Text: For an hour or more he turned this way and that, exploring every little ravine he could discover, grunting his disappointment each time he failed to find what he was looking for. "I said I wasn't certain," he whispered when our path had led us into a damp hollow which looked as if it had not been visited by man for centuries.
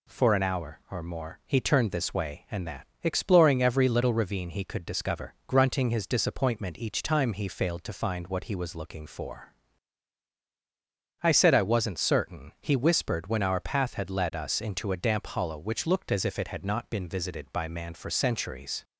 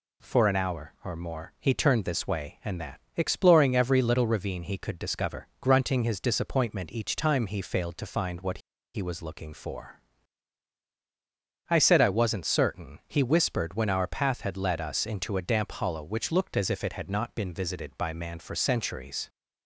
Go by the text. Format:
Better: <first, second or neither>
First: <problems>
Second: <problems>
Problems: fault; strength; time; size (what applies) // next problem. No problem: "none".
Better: first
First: none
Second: pauses between "what" and "he"; slight; at 8.5 s; 0.35 s long